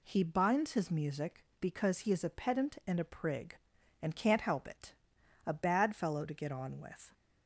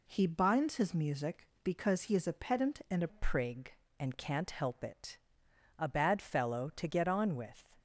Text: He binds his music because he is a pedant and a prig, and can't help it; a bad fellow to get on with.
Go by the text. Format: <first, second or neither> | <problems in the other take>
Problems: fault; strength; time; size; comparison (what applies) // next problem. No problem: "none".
first | changes voice at "prig"; from 3.0 s on; 4.6 s long